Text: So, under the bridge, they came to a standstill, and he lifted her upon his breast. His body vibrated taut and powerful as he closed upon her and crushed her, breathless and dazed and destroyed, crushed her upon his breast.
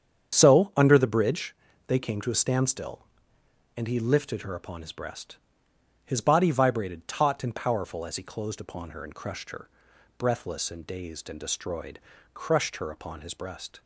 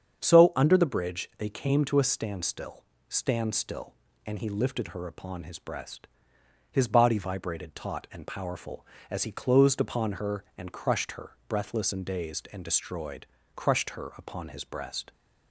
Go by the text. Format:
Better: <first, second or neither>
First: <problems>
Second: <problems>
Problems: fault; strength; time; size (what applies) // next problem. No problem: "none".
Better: first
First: starts louder than the rest; strong; until 1.4 s; 8 dB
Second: starts louder than the rest; strong; until 1.2 s; 7.5 dB // says "standstill" twice; at 3.0 s